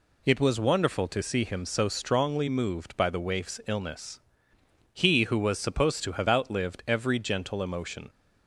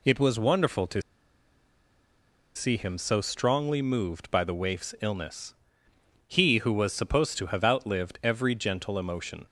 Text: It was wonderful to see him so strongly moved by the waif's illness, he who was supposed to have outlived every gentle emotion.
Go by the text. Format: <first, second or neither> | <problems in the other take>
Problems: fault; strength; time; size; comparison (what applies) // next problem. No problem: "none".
first | pauses between "to" and "see"; strong; at 1.0 s; 1.5 s long